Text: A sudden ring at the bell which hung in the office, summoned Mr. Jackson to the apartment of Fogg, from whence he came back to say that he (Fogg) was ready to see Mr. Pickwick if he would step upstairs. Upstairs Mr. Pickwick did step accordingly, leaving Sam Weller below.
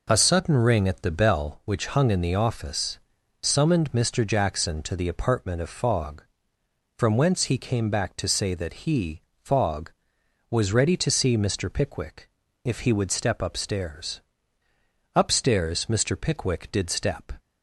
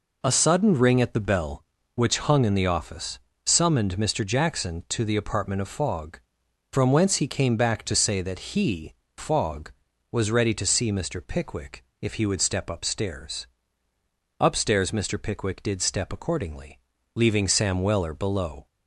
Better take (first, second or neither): second